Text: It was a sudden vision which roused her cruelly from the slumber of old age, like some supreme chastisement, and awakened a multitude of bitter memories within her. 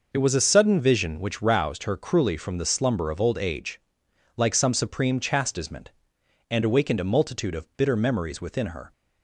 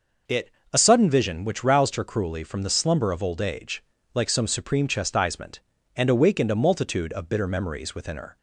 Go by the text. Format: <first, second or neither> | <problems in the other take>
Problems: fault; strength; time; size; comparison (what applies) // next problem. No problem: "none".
first | skips "was"; at 0.6 s